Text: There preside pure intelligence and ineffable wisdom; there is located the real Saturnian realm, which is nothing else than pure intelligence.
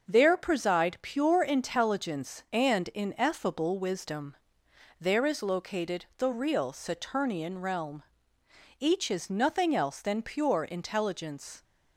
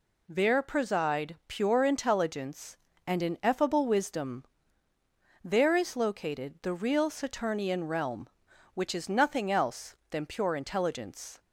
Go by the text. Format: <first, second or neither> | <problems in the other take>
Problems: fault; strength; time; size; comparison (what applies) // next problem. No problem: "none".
second | starts louder than the rest; until 1.1 s; 6.5 dB // says "each" for "which"; at 8.8 s